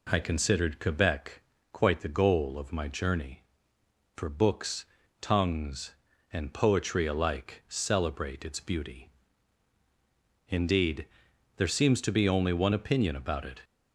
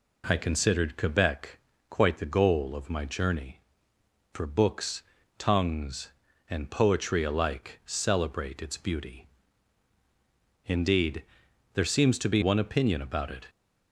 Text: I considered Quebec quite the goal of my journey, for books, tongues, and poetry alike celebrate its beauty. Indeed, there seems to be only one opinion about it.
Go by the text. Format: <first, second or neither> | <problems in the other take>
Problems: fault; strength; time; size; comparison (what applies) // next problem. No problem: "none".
first | pauses between "Quebec" and "quite"; slight; at 1.5 s; 0.32 s long; slight in the first // skips "only"; at 12.4 s